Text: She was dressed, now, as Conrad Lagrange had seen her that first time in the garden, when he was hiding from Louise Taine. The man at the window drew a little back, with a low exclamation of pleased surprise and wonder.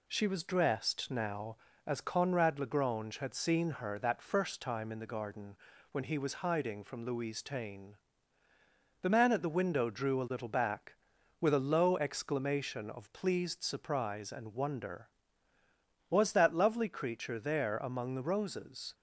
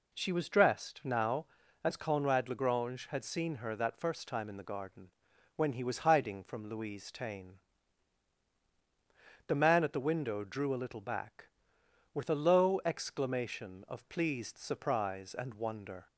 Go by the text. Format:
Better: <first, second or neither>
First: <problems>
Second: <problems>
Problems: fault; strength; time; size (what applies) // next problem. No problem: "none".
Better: second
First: goes on to say "Was that lovely creature there among the roses"; strong; from 16.0 s on; 2.8 s long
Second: none